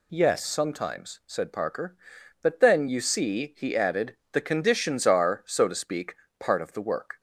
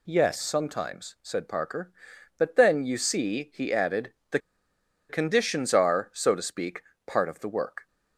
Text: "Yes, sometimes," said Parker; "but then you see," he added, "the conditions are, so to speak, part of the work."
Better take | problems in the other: first | pauses between "the" and "conditions"; noticeable; at 4.3 s; 0.70 s long

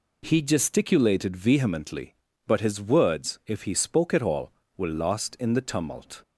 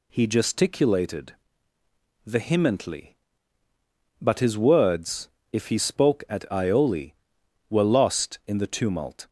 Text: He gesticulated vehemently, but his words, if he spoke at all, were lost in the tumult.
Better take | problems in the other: first | pauses between "gesticulated" and "vehemently"; noticeable; at 1.3 s; 0.90 s long // says "ioli" for "all"; at 6.4 s

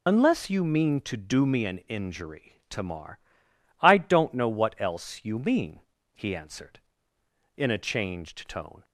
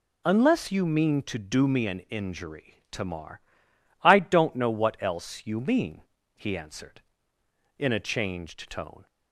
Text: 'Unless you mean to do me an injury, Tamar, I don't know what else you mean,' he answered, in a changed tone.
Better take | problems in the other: second | loses the start of "Unless"; at 0.0 s; 25 ms

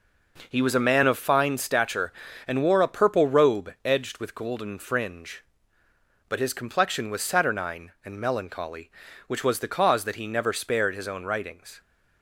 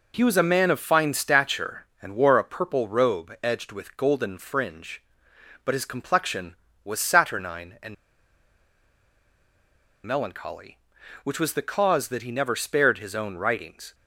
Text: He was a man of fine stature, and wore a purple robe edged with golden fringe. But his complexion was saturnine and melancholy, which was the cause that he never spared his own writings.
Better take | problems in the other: first | pauses between "and" and "melancholy"; strong; at 7.9 s; 2.1 s long

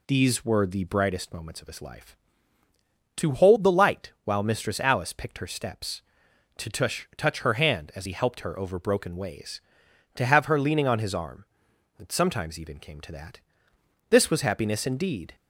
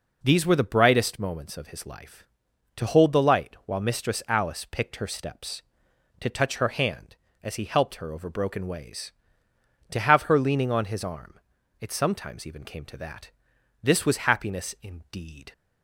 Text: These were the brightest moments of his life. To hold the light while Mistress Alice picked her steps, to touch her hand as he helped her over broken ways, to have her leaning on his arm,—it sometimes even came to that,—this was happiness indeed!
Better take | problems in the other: second | says "touch" twice; at 7.1 s

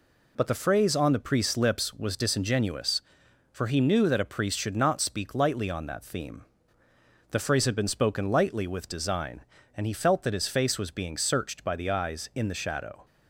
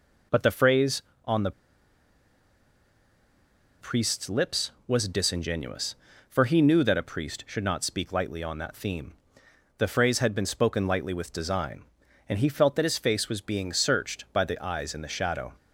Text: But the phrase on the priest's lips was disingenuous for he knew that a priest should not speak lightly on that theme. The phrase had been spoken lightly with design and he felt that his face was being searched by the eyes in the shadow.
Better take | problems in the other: first | pauses between "the" and "priest's"; strong; at 1.5 s; 2.2 s long

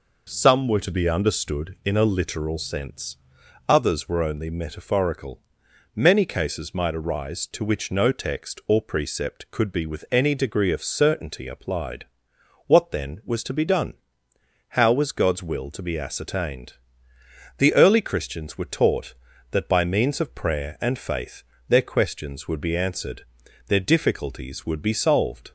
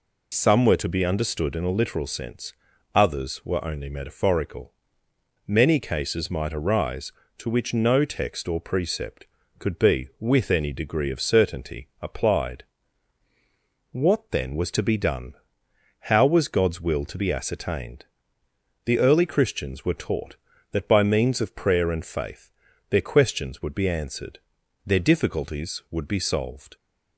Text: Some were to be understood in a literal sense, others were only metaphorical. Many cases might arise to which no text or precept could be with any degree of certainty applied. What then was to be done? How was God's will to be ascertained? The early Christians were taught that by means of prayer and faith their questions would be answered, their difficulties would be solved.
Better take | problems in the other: first | loses the start of "Some"; at 0.3 s; 30 ms // pauses between "faith" and "their"; at 22.5 s; 0.38 s long; slight in the first

